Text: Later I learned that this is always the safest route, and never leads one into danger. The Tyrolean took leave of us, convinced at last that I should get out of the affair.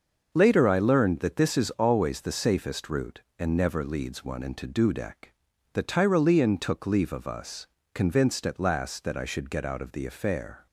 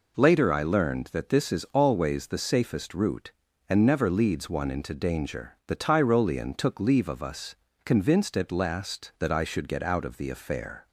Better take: second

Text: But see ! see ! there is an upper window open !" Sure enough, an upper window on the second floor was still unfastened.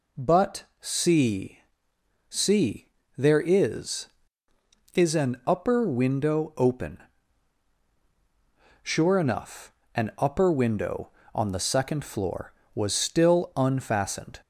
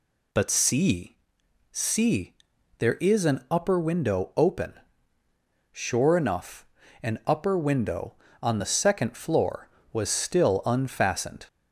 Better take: second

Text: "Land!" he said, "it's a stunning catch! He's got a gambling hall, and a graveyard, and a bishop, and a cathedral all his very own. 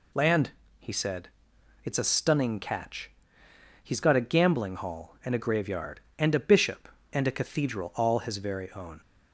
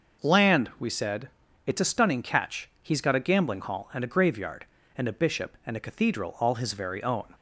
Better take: first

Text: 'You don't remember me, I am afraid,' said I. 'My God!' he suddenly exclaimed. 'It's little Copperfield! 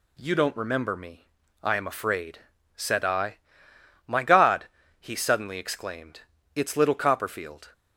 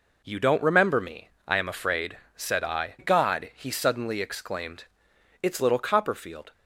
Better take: first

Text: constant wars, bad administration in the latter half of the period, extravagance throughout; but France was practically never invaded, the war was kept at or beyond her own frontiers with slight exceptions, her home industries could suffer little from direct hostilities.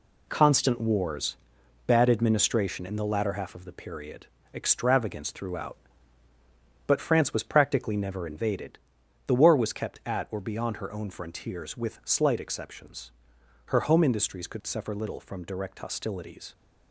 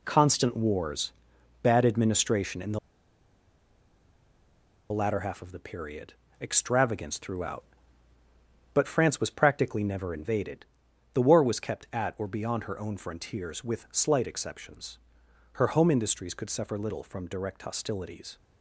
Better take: first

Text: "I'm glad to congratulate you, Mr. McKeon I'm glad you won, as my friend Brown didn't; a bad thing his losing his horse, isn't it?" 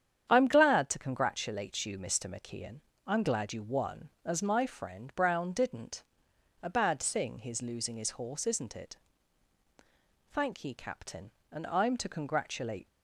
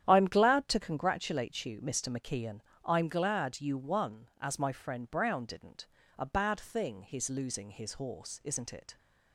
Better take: second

